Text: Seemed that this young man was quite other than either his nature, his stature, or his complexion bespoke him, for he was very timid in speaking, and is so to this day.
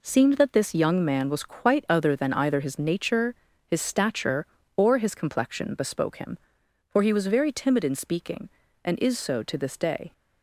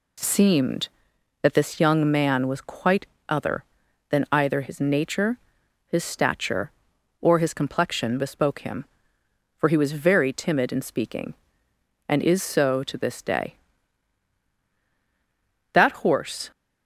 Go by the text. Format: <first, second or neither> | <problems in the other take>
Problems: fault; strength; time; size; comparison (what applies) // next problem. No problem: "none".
first | pauses between "quite" and "other"; slight; at 3.0 s; 0.22 s long // goes on to say "That horse"; noticeable; from 15.7 s on; 0.80 s long